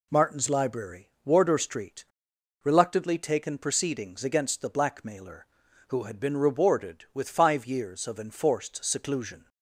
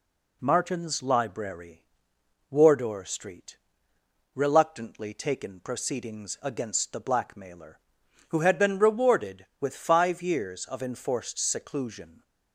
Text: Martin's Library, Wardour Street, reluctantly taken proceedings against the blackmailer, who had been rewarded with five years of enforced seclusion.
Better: neither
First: none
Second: none

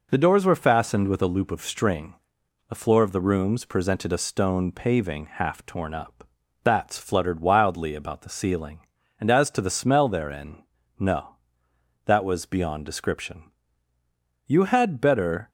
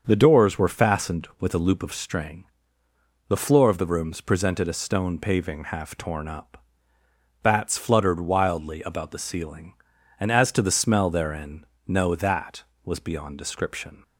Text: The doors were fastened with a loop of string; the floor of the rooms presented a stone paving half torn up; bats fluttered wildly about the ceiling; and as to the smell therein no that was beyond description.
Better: second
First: pauses between "therein" and "no"; slight; at 10.6 s; 0.36 s long // goes on to say "You had better"; noticeable; from 14.4 s on; 1.0 s long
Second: pauses between "therein" and "no"; slight; at 11.6 s; 0.24 s long

